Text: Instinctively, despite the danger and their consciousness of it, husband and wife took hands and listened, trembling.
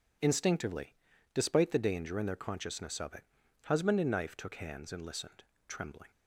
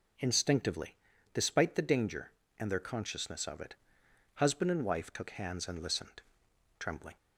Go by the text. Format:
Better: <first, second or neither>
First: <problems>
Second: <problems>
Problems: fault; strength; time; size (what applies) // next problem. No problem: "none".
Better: second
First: says "knife" for "wife"; at 4.1 s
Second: none